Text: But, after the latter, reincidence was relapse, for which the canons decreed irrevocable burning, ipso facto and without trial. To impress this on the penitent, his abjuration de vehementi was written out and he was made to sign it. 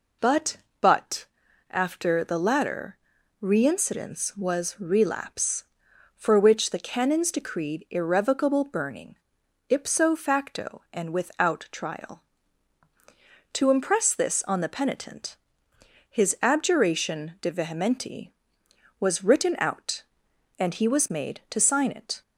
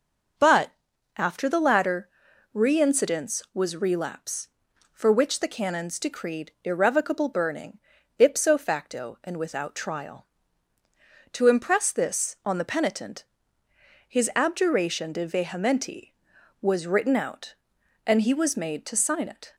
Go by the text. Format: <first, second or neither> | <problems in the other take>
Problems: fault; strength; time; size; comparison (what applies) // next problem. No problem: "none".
second | says "But" twice; at 0.8 s